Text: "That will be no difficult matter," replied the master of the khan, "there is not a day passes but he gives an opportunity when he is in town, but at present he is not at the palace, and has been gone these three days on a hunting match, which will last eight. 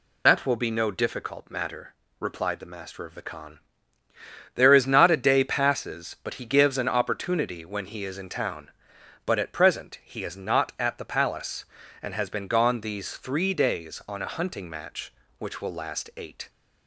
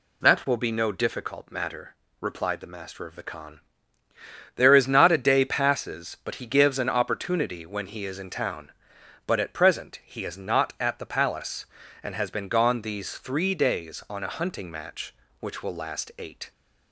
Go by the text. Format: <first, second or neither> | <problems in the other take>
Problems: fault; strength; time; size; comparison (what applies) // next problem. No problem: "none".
second | loses the start of "That"; at 0.2 s; 30 ms